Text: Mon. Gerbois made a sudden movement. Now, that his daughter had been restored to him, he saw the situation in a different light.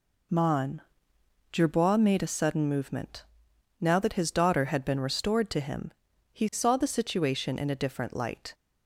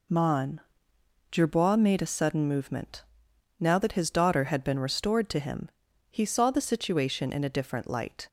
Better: neither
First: none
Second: none

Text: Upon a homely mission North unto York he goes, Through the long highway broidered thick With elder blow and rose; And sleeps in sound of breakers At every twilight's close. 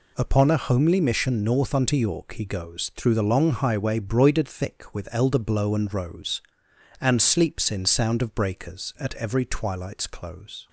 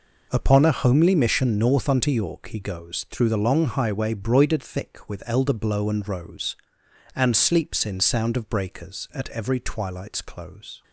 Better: first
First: none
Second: starts louder than the rest; noticeable; until 2.1 s; 5 dB

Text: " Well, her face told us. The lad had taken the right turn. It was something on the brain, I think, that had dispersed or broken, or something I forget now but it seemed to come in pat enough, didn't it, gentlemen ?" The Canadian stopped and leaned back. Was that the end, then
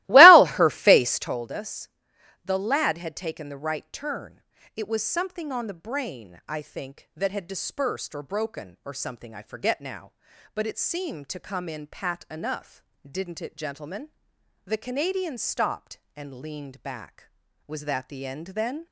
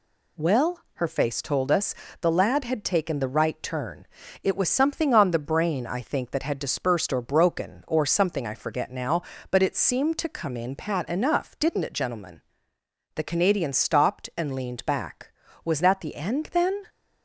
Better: second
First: starts louder than the rest; strong; until 1.4 s; 18.5 dB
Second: none

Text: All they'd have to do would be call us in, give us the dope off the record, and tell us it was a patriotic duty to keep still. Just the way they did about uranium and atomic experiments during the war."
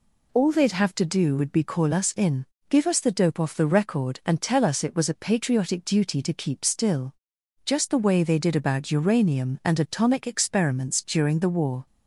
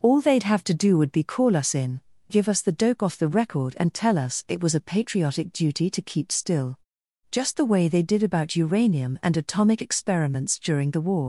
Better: first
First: none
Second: leaves "war" unfinished; at 11.2 s; 105 ms

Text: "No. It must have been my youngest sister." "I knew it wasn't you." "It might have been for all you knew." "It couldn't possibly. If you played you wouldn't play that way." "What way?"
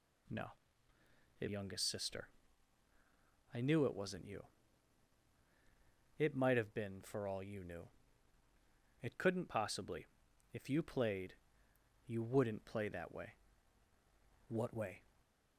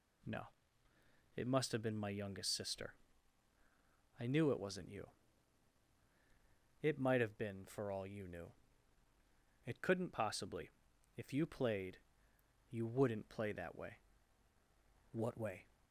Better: second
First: skips "must have been my"; at 1.4 s // pauses between "played" and "you"; noticeable; at 11.3 s; 0.72 s long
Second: pauses between "played" and "you"; noticeable; at 11.9 s; 0.72 s long

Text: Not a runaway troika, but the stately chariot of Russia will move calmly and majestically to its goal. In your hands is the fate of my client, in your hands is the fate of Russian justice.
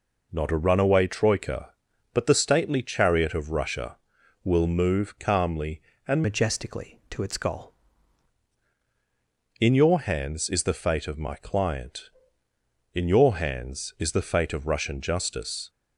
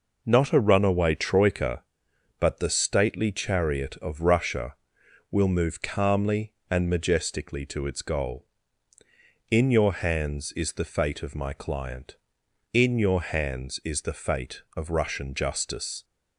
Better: second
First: changes voice from "majestically" to "goal"; from 6.2 to 7.7 s; 1.5 s long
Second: none

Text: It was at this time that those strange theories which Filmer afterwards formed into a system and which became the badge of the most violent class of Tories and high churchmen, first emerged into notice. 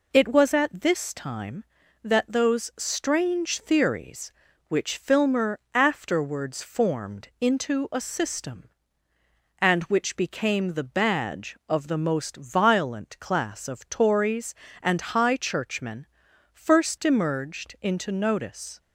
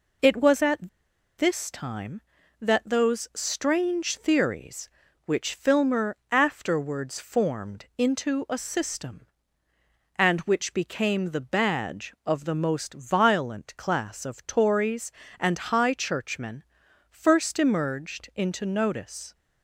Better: first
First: none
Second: pauses between "at" and "this"; noticeable; at 0.8 s; 0.48 s long

